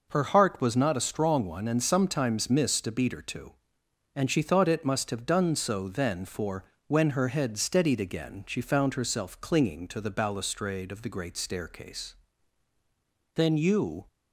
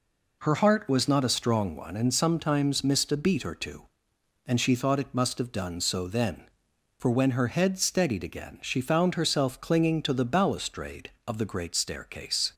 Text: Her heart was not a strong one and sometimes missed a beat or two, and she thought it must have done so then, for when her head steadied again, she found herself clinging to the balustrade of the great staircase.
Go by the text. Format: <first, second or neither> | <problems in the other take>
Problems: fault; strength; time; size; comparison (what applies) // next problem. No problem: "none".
second | pauses between "for" and "when"; slight; at 6.6 s; 0.24 s long // goes on to say "Then you"; noticeable; from 13.3 s on; 0.72 s long